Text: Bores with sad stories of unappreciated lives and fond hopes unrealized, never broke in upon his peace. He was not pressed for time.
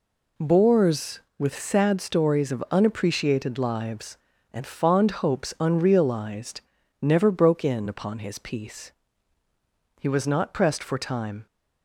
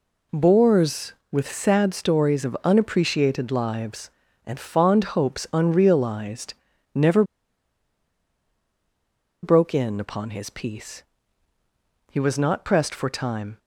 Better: first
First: none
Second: pauses between "never" and "broke"; strong; at 7.2 s; 2.1 s long

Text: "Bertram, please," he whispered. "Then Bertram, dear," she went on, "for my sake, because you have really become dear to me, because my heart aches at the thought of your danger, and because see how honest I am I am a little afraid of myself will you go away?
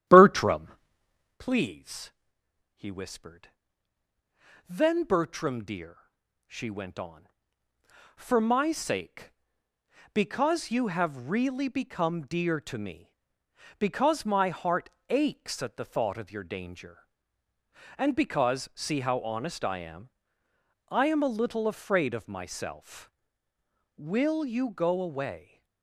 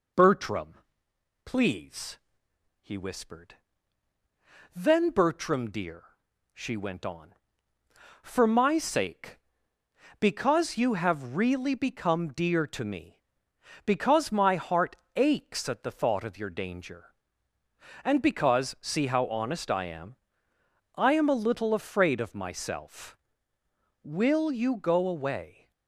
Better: second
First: starts louder than the rest; strong; until 1.4 s; 11.5 dB // pauses between "heart" and "aches"; slight; at 14.8 s; 0.22 s long // pauses between "am" and "I"; noticeable; at 20.0 s; 0.80 s long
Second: pauses between "heart" and "aches"; slight; at 14.9 s; 0.22 s long // pauses between "am" and "I"; noticeable; at 20.1 s; 0.80 s long

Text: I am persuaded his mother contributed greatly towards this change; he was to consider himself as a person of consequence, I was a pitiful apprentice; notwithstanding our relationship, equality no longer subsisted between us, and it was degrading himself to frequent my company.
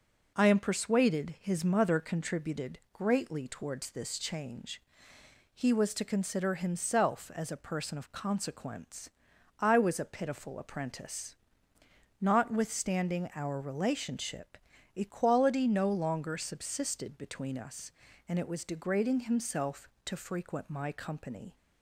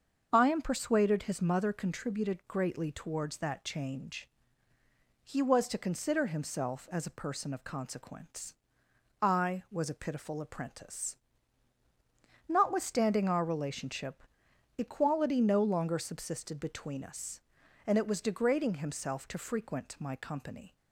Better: first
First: none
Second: starts louder than the rest; until 1.3 s; 6.5 dB // says "that" for "this"; at 3.3 s

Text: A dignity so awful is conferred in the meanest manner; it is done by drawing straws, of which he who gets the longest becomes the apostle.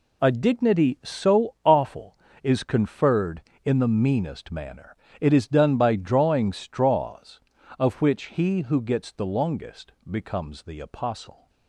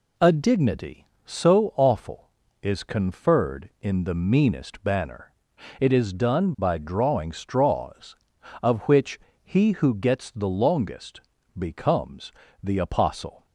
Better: first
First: pauses between "longest" and "becomes"; slight; at 9.9 s; 0.18 s long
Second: says "banner" for "manner"; at 4.8 s // pauses between "which" and "he"; slight; at 9.1 s; 0.28 s long // pauses between "longest" and "becomes"; slight; at 11.2 s; 0.36 s long // pauses between "becomes" and "the"; slight; at 12.3 s; 0.28 s long

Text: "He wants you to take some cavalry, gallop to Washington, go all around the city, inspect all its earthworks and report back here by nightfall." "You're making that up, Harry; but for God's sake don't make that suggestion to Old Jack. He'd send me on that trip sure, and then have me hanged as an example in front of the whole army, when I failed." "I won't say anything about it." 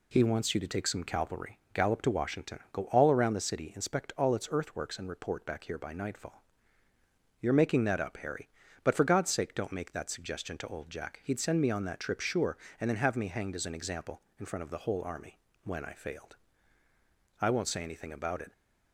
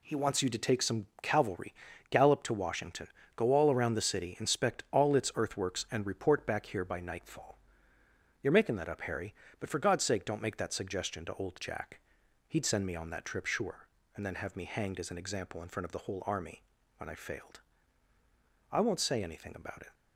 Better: neither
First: none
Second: none

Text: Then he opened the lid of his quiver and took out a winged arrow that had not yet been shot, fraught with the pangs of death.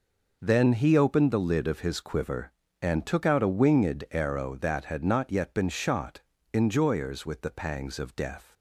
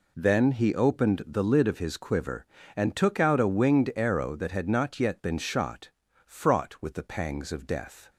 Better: second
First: says "enjoyers" for "fraught"; at 6.5 s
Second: none

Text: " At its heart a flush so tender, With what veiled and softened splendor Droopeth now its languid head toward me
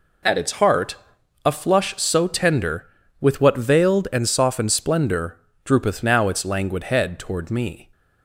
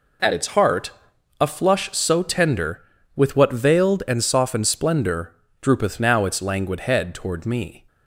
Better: neither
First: pauses between "heart" and "a"; noticeable; at 0.9 s; 0.48 s long // pauses between "splendor" and "Droopeth"; slight; at 5.3 s; 0.26 s long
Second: pauses between "heart" and "a"; noticeable; at 0.9 s; 0.48 s long // pauses between "splendor" and "Droopeth"; slight; at 5.3 s; 0.28 s long

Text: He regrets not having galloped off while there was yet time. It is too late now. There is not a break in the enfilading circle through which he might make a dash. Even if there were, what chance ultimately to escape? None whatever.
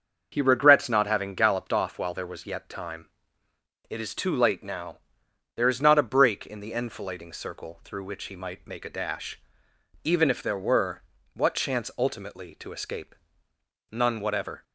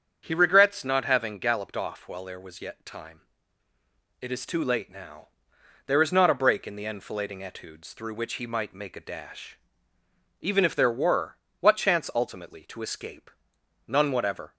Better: first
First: starts louder than the rest; until 1.3 s; 6.5 dB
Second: starts louder than the rest; strong; until 1.2 s; 7.5 dB // says "etudes" for "circle"; at 7.4 s

